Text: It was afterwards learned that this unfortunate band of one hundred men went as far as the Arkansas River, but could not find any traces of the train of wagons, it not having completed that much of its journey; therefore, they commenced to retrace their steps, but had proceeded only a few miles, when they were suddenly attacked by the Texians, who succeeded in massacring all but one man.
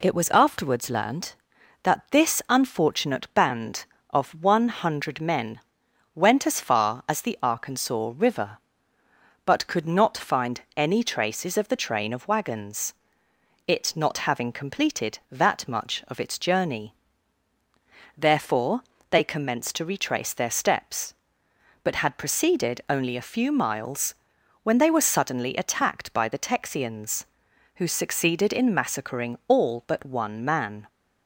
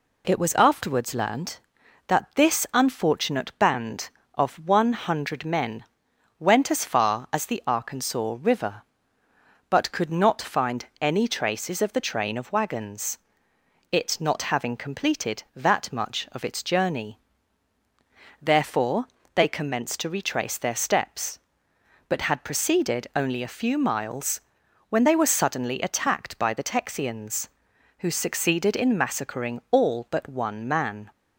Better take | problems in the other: neither | pauses between "men" and "went"; noticeable; the same in both

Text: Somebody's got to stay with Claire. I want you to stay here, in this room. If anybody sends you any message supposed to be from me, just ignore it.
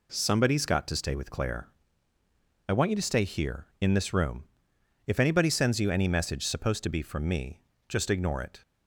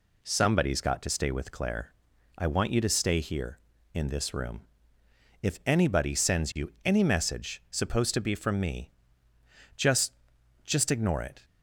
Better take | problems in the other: first | says "just" twice; at 10.6 s

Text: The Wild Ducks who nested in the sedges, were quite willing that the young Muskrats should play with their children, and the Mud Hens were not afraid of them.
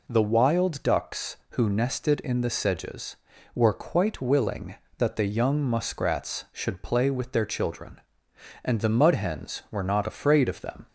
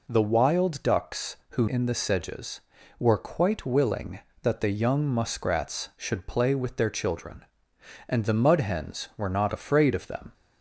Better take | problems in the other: first | skips "nested"; at 1.6 s

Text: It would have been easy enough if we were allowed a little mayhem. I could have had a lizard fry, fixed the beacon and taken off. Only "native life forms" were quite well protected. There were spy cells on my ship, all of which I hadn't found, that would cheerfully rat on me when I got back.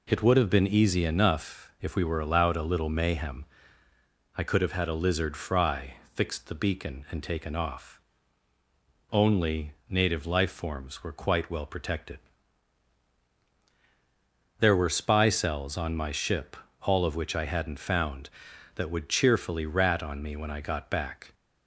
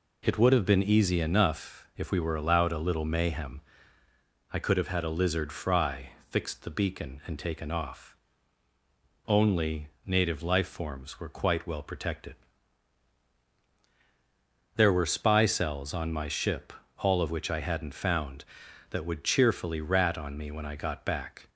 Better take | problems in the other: neither | pauses between "Only" and "native"; slight; the same in both

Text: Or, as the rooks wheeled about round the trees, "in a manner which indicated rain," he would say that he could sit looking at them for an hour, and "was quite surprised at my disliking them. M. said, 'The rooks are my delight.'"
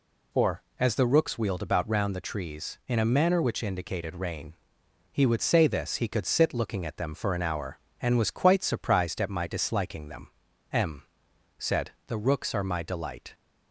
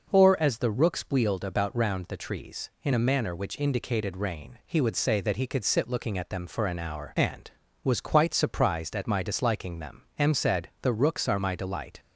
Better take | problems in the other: second | says "this" for "that"; at 5.6 s

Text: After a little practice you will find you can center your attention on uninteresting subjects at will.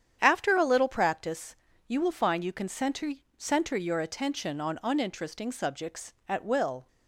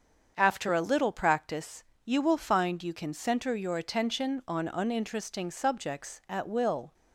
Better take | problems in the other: second | starts louder than the rest; strong; until 1.2 s; 9 dB; also in the second // pauses between "practice" and "you"; slight; at 1.5 s; 0.32 s long; slight in the second // says "center" twice; at 3.3 s

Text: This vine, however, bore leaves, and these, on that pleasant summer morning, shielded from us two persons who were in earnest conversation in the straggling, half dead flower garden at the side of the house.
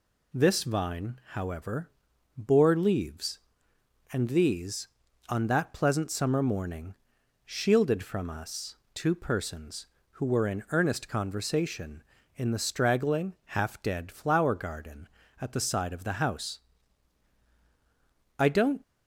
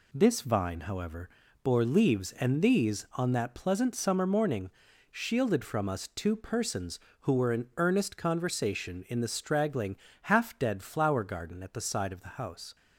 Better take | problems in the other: second | pauses between "us" and "two"; slight; at 8.7 s; 0.18 s long // goes on to say "I don't"; slight; from 18.3 s on; 0.44 s long

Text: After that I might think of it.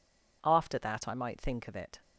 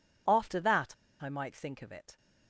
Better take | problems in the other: first | pauses between "that" and "I"; slight; at 0.9 s; 0.28 s long

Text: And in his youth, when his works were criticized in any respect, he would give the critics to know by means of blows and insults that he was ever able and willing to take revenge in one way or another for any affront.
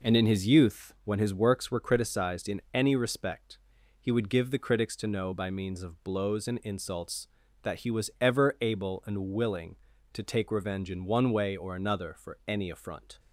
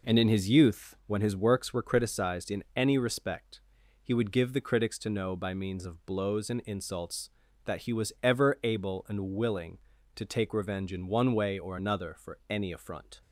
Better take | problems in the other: neither | none

